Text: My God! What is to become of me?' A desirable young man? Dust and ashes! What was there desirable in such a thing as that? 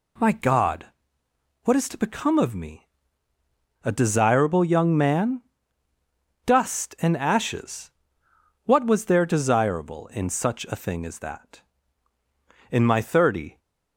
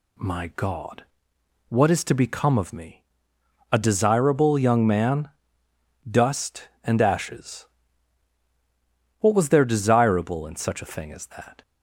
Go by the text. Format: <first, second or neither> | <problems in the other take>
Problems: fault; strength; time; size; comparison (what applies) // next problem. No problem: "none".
second | goes on to say "In my thirty"; noticeable; from 12.7 s on; 0.88 s long